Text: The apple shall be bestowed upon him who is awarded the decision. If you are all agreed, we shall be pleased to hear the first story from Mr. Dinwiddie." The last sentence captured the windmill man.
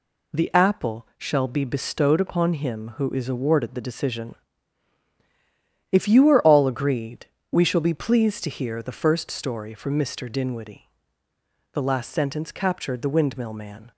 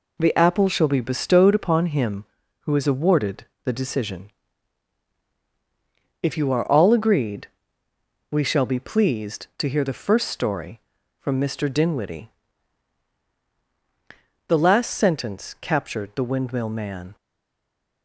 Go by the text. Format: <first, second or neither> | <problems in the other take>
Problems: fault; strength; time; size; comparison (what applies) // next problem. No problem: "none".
first | pauses between "awarded" and "the"; slight; at 3.4 s; 0.18 s long // stays silent after the last word; slight; from 17.1 s on; 0.9 s long